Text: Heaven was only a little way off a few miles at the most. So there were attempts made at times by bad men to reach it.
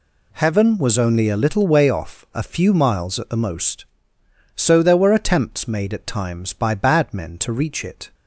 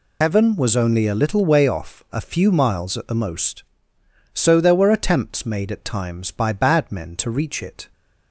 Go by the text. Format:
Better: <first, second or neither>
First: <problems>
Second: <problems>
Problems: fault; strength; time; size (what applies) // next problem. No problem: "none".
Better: first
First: none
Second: loses the start of "Heaven"; at 0.2 s; 100 ms